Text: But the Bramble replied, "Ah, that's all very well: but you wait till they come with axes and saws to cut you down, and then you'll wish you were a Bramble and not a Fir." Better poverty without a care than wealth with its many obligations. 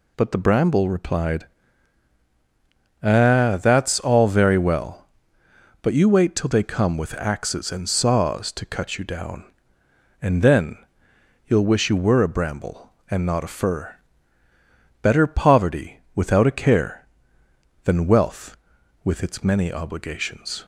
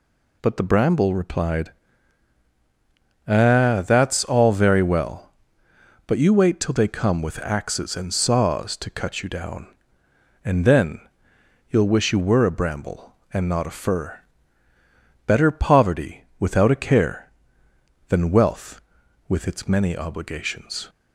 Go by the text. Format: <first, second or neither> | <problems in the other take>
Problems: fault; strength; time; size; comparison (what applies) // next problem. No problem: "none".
neither | pauses between "then" and "you'll"; noticeable; the same in both